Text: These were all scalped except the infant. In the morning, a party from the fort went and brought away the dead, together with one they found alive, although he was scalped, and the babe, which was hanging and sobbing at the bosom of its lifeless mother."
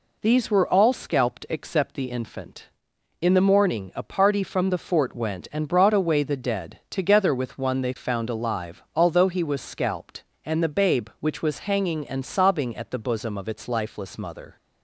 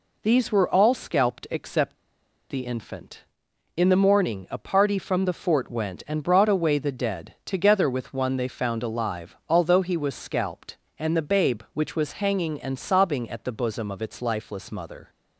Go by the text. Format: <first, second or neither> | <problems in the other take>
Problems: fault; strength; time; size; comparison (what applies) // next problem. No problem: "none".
first | pauses between "except" and "the"; noticeable; at 1.9 s; 0.54 s long